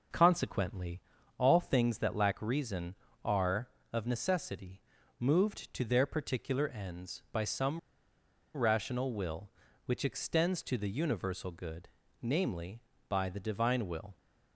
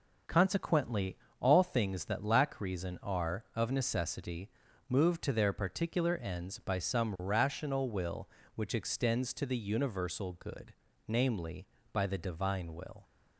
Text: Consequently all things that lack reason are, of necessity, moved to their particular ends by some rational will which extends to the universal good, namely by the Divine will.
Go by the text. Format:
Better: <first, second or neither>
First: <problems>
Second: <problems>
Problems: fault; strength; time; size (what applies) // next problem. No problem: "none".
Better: second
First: pauses between "Consequently" and "all"; at 0.9 s; 0.38 s long // pauses between "some" and "rational"; noticeable; at 7.7 s; 0.77 s long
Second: pauses between "Consequently" and "all"; slight; at 1.1 s; 0.24 s long